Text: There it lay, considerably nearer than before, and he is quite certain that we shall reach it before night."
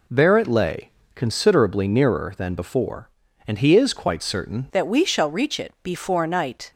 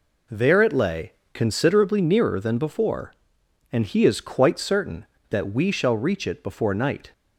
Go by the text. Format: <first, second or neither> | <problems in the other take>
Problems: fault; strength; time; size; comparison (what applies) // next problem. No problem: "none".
second | changes voice at "that"; from 4.7 s on; 2.0 s long